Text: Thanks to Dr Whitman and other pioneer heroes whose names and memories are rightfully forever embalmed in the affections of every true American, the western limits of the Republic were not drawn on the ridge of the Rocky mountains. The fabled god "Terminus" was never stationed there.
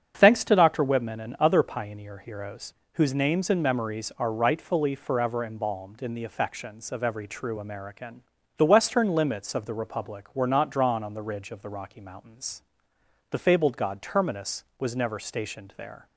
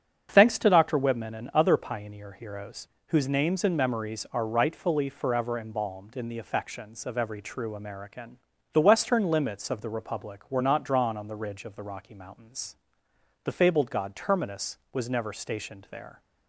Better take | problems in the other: neither | starts louder than the rest; strong; the same in both // pauses between "heroes" and "whose"; slight; the same in both

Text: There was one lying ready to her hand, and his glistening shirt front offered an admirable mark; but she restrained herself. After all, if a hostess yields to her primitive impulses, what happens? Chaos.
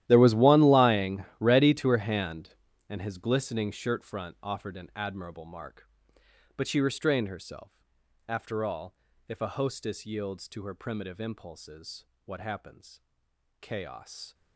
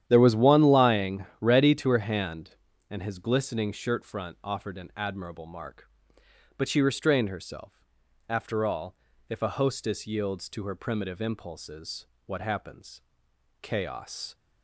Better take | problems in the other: second | gets quieter; strong; throughout; 16.5 dB // starts louder than the rest; strong; until 1.0 s; 13 dB; strong in the second // pauses between "lying" and "ready"; slight; at 1.2 s; 0.16 s long; slight in the second

